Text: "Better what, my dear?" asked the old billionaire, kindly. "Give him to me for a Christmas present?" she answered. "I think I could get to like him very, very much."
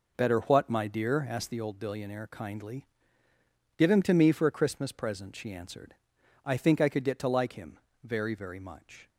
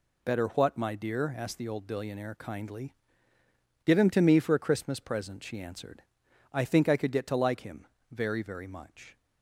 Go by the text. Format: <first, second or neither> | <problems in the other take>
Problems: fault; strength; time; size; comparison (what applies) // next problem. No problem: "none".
second | starts louder than the rest; noticeable; until 1.8 s; 4.5 dB // pauses between "him" and "very"; slight; at 7.7 s; 0.24 s long; slight in the second